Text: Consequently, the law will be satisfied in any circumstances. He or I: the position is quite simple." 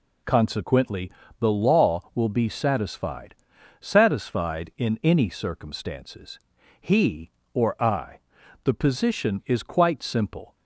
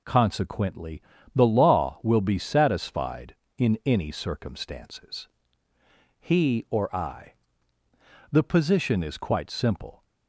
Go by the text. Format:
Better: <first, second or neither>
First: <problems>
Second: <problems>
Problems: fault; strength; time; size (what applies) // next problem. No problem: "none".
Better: second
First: says "satisfied" twice; at 3.8 s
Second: none